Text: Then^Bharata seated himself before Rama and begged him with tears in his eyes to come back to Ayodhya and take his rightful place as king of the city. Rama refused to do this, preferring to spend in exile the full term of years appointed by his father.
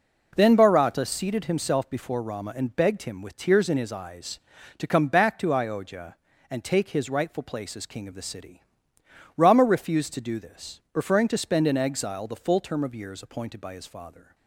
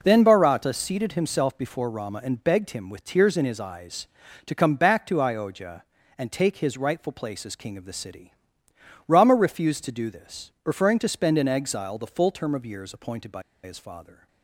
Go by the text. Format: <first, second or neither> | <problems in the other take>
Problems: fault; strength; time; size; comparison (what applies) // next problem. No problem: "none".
first | pauses between "by" and "his"; slight; at 13.4 s; 0.22 s long